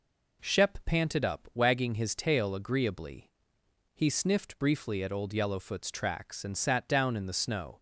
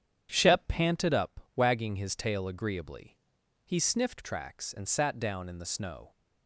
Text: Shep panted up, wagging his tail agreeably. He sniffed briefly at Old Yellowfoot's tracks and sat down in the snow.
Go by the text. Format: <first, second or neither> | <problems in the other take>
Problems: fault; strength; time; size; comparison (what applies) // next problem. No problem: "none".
first | starts louder than the rest; strong; until 1.3 s; 9 dB // skips "briefly at Old Yellowfoot's"; at 4.2 s